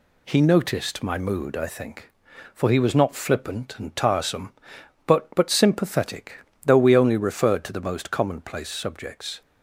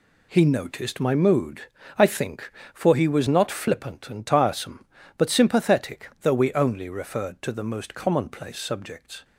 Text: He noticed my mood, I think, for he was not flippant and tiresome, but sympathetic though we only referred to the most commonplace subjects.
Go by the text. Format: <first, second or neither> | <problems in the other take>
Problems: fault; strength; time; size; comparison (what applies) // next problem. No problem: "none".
second | says "but" twice; at 5.3 s // pauses between "sympathetic" and "though"; slight; at 6.3 s; 0.26 s long